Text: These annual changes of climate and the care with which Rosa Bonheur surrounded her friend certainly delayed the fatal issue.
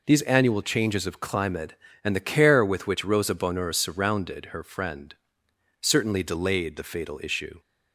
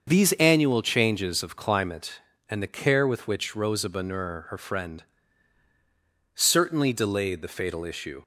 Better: first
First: pauses between "friend" and "certainly"; noticeable; at 5.1 s; 0.66 s long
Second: starts louder than the rest; until 1.0 s; 6.5 dB // skips "surrounded"; at 4.4 s // pauses between "friend" and "certainly"; strong; at 5.0 s; 1.3 s long

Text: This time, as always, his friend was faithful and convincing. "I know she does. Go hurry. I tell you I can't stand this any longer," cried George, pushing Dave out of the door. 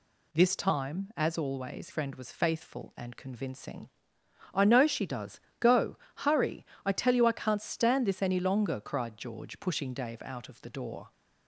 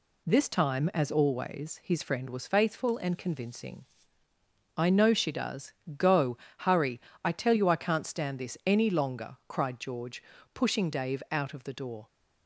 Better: second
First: skips "his"; at 1.8 s // pauses between "Go" and "hurry"; slight; at 5.9 s; 0.30 s long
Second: pauses between "Go" and "hurry"; slight; at 6.3 s; 0.22 s long

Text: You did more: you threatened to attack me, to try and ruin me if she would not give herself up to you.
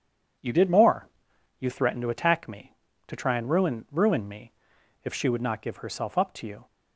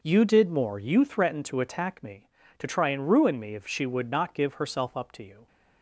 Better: second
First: says "ruin" twice; at 3.9 s // pauses between "me" and "if"; noticeable; at 4.5 s; 0.50 s long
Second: none

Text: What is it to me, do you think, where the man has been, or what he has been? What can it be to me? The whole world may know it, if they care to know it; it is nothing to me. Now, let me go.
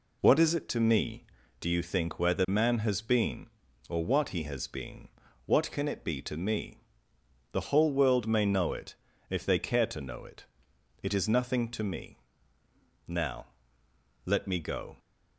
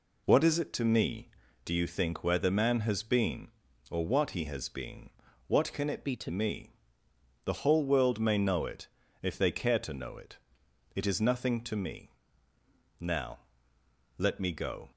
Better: first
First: none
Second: changes voice from "be" to "to"; from 6.0 to 6.2 s; 0.2 s long

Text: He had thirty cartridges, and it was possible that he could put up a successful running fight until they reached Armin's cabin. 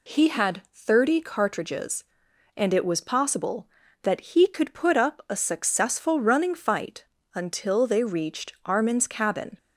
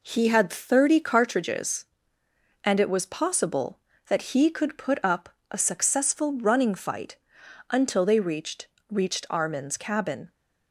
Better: first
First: pauses between "fight" and "until"; slight; at 7.0 s; 0.32 s long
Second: pauses between "up" and "a"; slight; at 5.2 s; 0.22 s long // pauses between "fight" and "until"; noticeable; at 7.1 s; 0.54 s long // says "reached" twice; at 8.9 s

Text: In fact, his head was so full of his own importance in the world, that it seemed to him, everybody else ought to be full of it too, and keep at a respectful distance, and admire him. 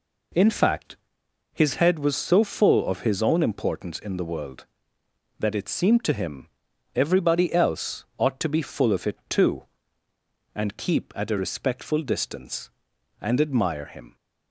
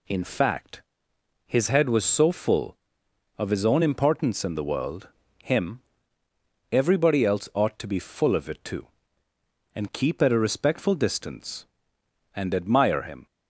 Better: first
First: none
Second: skips "that it seemed to"; at 5.2 s

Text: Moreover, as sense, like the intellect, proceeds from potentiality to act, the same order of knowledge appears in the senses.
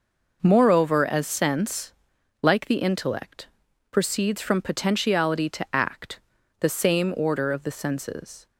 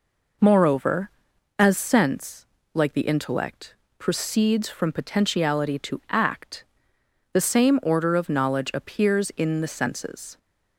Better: second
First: skips "knowledge appears in"; at 7.6 s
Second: none

